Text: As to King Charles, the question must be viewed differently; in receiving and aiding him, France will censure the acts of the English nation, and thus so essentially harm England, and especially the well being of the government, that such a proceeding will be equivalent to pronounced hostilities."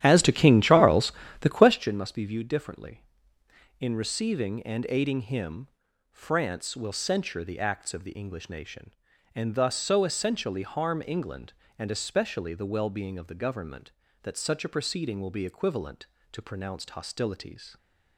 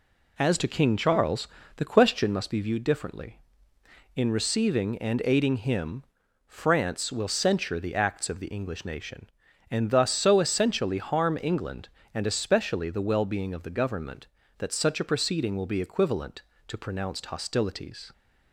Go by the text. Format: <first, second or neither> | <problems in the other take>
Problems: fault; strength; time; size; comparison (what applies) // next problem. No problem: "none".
second | starts louder than the rest; strong; until 1.8 s; 11.5 dB